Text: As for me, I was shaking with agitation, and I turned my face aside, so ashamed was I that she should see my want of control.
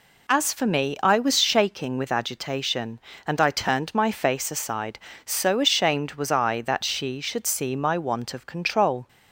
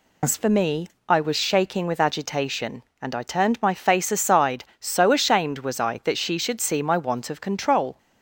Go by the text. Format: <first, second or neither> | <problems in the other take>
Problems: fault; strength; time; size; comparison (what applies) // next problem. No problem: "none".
first | loses the start of "As"; at 0.2 s; 85 ms